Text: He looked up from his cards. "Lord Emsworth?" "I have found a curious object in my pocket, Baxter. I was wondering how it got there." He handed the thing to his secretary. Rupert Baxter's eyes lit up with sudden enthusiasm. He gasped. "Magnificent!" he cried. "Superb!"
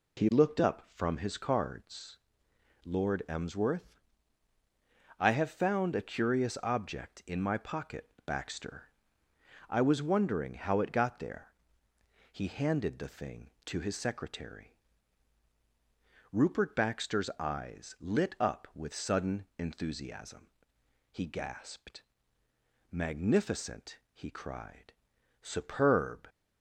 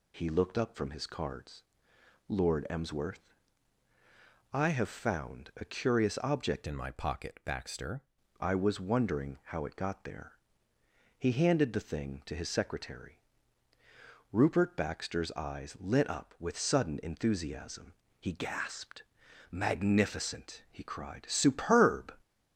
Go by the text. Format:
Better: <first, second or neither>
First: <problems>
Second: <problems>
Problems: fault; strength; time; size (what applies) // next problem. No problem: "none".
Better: first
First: none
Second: changes voice from "in" to "Baxter"; from 6.6 to 8.0 s; 1.4 s long